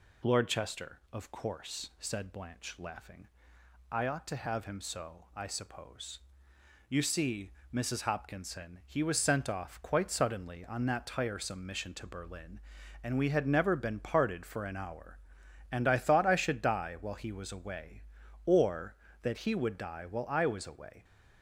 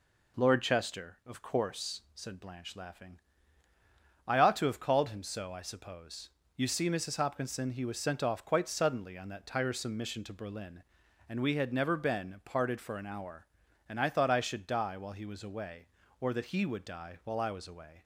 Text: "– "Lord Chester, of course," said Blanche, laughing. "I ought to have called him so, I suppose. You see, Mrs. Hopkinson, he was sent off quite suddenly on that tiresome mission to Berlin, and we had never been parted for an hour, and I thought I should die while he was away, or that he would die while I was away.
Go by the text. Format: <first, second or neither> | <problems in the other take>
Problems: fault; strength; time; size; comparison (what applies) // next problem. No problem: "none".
second | skips "called"; at 4.6 s